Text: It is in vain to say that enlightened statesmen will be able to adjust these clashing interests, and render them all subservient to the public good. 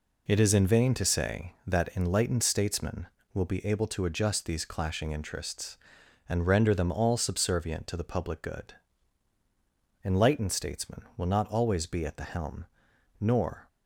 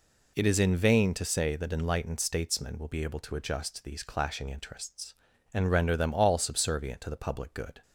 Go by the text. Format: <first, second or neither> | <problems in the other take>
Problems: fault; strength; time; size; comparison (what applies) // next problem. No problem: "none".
second | goes on to say "Enlightened statesmen will not always be at the helm Nor"; strong; from 10.0 s on; 3.6 s long